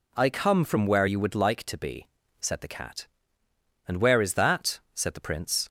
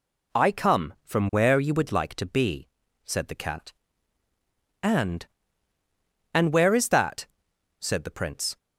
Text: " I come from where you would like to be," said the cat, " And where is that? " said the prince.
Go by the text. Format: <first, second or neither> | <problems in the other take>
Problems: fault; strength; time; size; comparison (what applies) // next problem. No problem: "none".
first | says "And" twice; at 6.3 s